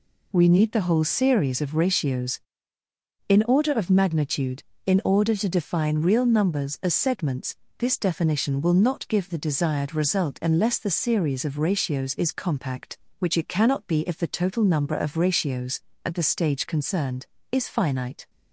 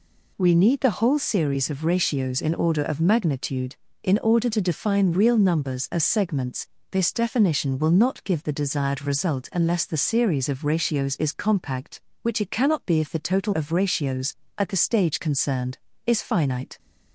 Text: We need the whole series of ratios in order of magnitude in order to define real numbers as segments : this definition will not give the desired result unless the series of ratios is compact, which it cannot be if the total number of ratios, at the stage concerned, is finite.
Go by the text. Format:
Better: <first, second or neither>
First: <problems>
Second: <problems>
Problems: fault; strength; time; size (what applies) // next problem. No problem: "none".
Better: first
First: none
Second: skips "number"; at 13.5 s